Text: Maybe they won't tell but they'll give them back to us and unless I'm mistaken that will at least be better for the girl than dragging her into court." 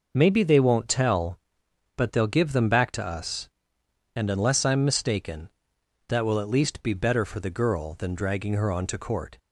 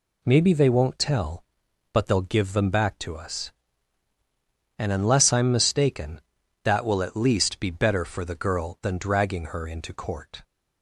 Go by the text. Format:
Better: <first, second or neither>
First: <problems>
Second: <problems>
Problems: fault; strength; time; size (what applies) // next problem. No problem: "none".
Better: second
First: says "onto" for "into"; at 8.7 s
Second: none